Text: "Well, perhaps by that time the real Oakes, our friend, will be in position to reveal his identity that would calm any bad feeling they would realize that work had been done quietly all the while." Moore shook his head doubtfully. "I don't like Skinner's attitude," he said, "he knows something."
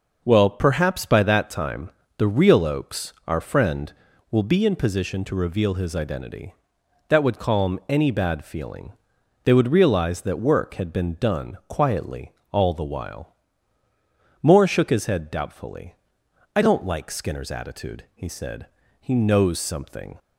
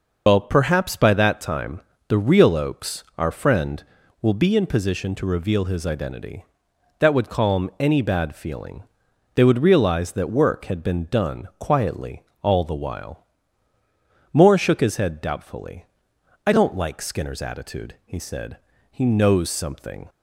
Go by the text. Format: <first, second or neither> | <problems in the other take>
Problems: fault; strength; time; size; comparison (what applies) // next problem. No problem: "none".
first | loses the start of "Well"; at 0.2 s; 115 ms // pauses between "time" and "the"; slight; at 1.8 s; 0.28 s long; slight in the first // pauses between "feeling" and "they"; noticeable; at 8.8 s; 0.52 s long; noticeable in the first // pauses between "quietly" and "all"; slight; at 12.2 s; 0.22 s long; slight in the first